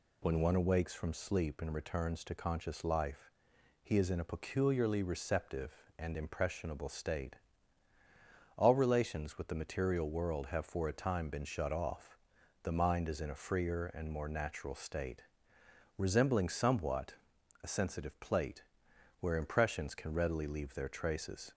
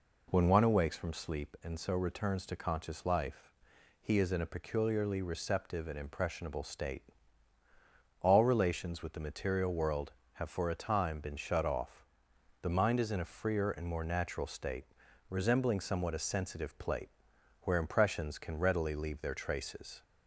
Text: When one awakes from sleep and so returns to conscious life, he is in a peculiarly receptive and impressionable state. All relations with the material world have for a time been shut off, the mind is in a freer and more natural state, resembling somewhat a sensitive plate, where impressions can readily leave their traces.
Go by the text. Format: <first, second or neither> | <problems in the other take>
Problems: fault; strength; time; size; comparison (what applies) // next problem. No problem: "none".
second | skips "so"; at 1.7 s // pauses between "somewhat" and "a"; noticeable; at 17.1 s; 0.48 s long